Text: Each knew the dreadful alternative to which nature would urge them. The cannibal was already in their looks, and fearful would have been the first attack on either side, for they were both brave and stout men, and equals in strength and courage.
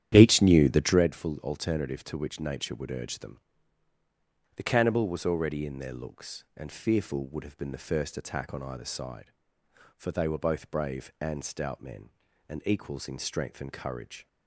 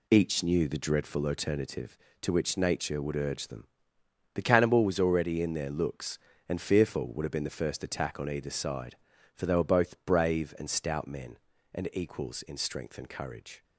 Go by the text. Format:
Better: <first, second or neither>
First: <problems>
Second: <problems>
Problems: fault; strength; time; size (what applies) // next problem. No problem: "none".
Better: second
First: starts louder than the rest; strong; until 1.0 s; 10.5 dB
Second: none